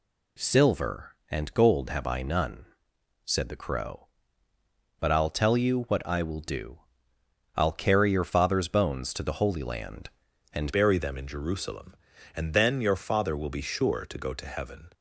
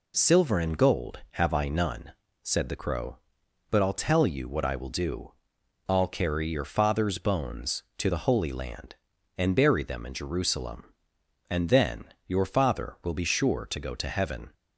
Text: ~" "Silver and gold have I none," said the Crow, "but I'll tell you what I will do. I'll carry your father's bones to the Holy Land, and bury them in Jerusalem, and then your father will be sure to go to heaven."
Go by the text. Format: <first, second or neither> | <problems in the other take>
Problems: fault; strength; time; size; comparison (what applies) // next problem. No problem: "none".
second | changes voice at "bury"; from 10.7 s on; 4.2 s long